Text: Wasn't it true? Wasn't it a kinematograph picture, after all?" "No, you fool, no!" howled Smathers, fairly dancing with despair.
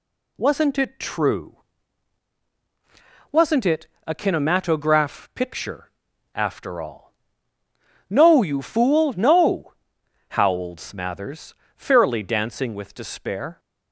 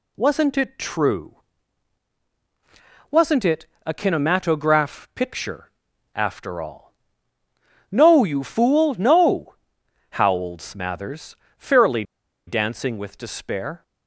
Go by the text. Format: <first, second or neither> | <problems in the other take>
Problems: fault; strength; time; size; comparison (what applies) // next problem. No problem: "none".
first | pauses between "it" and "a"; slight; at 3.6 s; 0.20 s long; slight in the first // pauses between "fairly" and "dancing"; at 12.0 s; 0.44 s long